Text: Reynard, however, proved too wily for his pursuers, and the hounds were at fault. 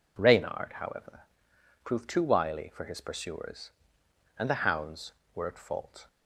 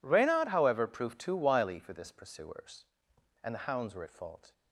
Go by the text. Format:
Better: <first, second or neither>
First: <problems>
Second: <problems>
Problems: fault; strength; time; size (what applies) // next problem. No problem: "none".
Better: first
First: none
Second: says "this" for "his"; at 1.9 s